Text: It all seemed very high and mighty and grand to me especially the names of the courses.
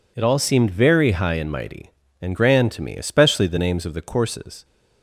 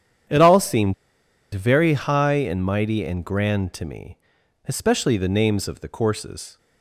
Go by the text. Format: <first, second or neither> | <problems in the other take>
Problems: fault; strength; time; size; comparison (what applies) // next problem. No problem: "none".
first | starts louder than the rest; strong; until 1.9 s; 9 dB // pauses between "seemed" and "very"; noticeable; at 0.9 s; 0.60 s long // pauses between "me" and "especially"; noticeable; at 4.1 s; 0.50 s long